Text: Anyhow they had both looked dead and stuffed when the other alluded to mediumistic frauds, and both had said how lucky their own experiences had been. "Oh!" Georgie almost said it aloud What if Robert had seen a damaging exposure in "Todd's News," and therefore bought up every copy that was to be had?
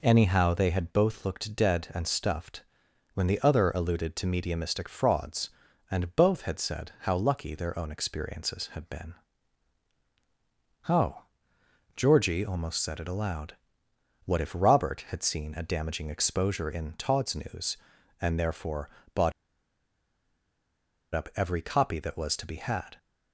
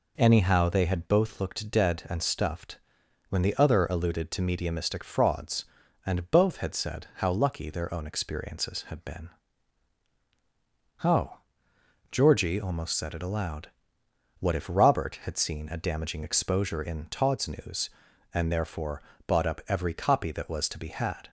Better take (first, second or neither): second